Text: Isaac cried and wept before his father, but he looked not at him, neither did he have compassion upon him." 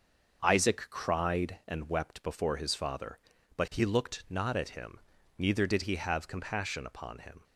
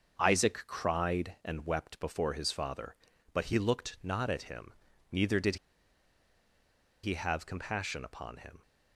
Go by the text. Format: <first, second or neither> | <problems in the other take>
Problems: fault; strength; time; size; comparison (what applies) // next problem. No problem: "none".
first | starts louder than the rest; until 1.2 s; 6.5 dB; also in the first // pauses between "did" and "he"; strong; at 5.5 s; 1.4 s long